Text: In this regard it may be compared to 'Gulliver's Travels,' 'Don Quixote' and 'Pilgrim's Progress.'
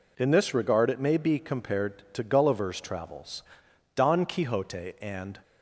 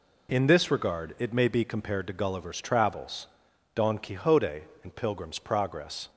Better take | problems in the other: second | stops before "Pilgrim's Progress"; at 5.4 s

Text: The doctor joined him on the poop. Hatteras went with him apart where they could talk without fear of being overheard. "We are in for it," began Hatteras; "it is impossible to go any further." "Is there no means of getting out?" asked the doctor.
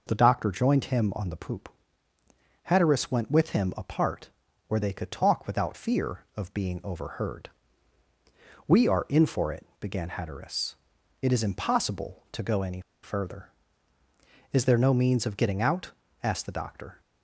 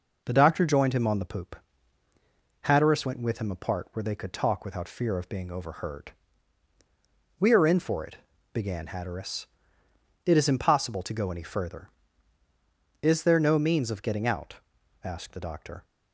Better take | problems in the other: second | pauses between "apart" and "where"; at 4.2 s; 0.38 s long // pauses between "any" and "further"; slight; at 12.7 s; 0.23 s long

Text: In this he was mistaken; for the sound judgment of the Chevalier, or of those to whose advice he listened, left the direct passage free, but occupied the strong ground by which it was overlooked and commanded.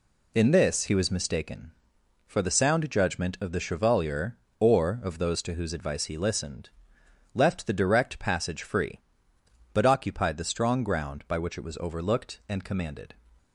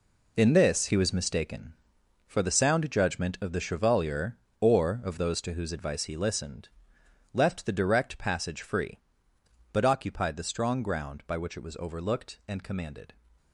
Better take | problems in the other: first | gets quieter; strong; throughout; 10 dB

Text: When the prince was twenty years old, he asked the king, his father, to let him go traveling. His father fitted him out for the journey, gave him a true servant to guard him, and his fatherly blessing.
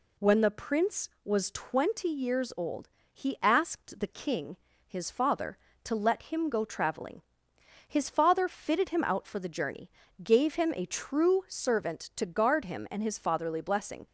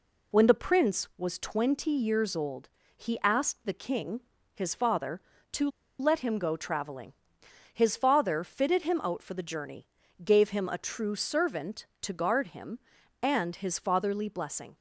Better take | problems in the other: first | pauses between "to" and "let"; slight; at 5.6 s; 0.31 s long

